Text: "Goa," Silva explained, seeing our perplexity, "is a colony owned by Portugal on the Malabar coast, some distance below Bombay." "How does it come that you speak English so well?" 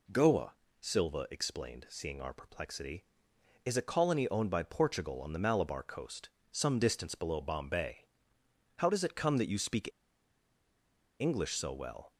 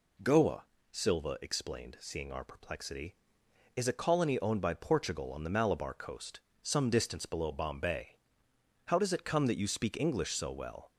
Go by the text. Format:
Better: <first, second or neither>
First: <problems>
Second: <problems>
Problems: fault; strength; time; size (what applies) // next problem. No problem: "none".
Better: second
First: pauses between "speak" and "English"; strong; at 9.8 s; 1.3 s long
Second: none